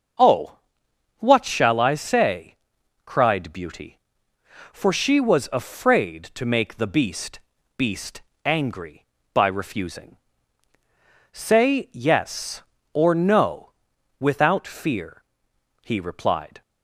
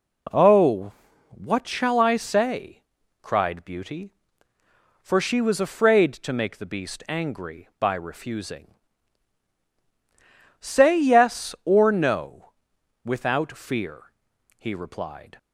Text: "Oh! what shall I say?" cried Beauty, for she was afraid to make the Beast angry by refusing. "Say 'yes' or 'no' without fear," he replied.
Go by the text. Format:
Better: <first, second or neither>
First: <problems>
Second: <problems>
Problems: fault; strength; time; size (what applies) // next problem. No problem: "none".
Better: second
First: starts louder than the rest; noticeable; until 1.7 s; 6 dB // says "Beast" twice; at 7.7 s // pauses between "no" and "without"; noticeable; at 13.7 s; 0.48 s long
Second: pauses between "no" and "without"; noticeable; at 12.5 s; 0.54 s long